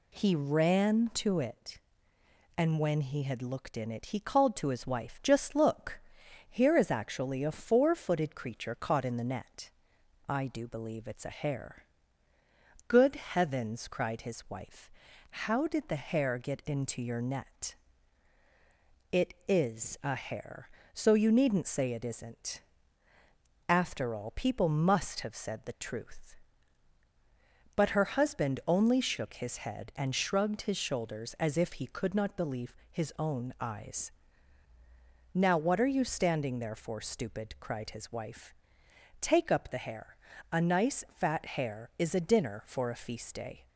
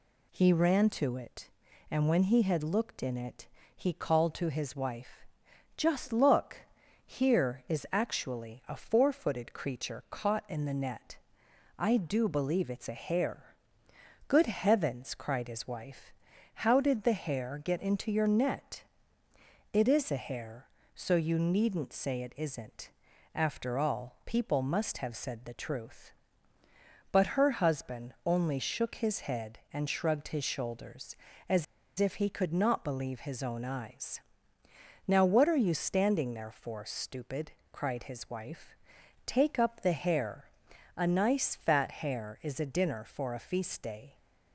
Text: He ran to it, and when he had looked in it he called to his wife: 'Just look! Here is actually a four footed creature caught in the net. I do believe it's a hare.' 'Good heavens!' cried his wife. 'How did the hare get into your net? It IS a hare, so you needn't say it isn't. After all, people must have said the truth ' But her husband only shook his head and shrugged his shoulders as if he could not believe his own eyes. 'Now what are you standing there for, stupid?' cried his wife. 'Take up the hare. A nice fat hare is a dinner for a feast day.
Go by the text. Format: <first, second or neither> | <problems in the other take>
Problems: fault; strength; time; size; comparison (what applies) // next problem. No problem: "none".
first | pauses between "it" and "he"; slight; at 3.4 s; 0.28 s long // pauses between "as" and "if"; slight; at 31.6 s; 0.34 s long